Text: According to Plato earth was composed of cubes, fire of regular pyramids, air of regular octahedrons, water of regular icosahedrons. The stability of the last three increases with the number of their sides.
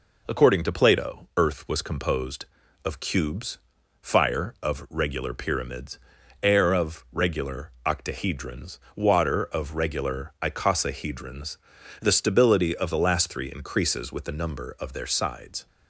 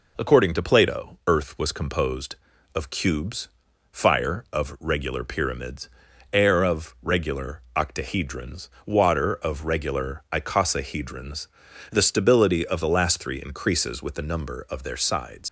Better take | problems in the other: first | leaves "sides" unfinished; at 15.4 s; 80 ms

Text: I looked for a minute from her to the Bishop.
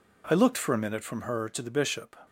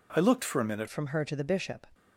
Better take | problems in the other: first | changes voice at "from"; from 0.8 s on; 1.0 s long

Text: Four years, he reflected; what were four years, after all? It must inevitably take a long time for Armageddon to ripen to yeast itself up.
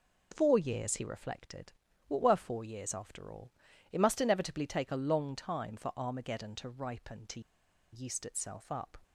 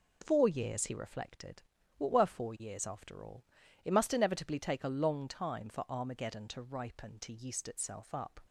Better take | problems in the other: second | pauses between "to" and "yeast"; noticeable; at 7.4 s; 0.52 s long

